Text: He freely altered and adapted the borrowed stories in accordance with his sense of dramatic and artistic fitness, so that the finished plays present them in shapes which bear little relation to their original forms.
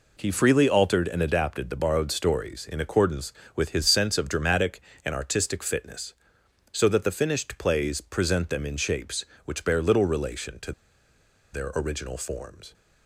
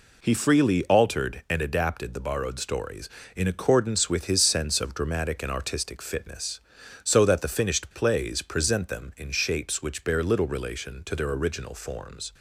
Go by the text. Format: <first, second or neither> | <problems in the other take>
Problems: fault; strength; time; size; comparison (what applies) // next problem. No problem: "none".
second | pauses between "to" and "their"; noticeable; at 10.7 s; 0.81 s long